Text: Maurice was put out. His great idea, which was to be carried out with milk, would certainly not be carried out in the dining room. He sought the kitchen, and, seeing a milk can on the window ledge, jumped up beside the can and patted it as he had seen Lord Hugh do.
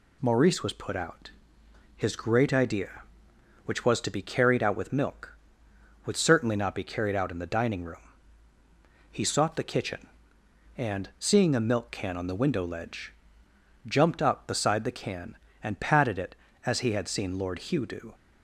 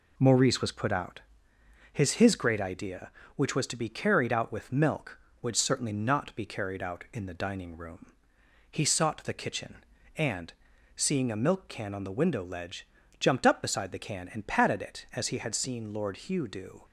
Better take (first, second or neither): first